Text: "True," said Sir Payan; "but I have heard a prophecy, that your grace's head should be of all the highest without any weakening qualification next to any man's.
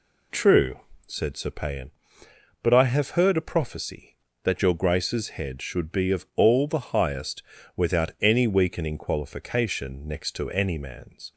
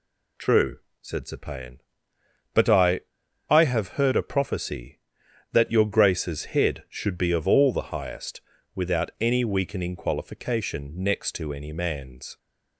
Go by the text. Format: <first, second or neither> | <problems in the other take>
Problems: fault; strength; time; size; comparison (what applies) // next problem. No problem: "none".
first | says "I" twice; at 3.4 s // pauses between "highest" and "without"; slight; at 8.4 s; 0.32 s long; slight in the first